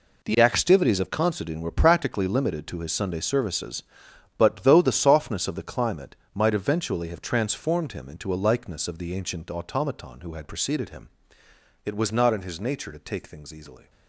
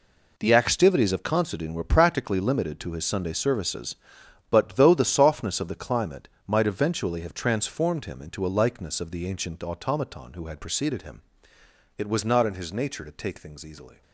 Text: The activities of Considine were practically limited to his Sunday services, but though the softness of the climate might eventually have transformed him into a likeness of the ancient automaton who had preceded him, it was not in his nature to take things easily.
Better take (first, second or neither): neither